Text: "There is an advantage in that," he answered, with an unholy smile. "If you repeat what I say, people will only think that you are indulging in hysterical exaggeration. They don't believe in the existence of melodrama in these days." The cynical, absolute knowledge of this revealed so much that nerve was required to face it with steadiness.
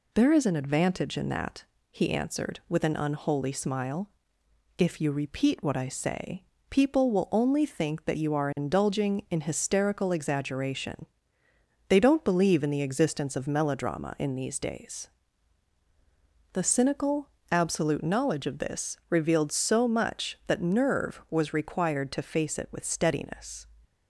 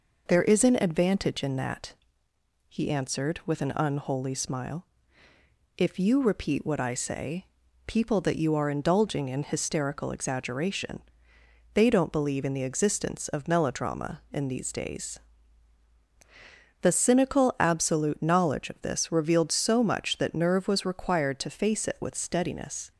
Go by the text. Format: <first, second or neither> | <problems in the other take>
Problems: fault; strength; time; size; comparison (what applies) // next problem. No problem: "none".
first | skips "will only think"; at 8.2 s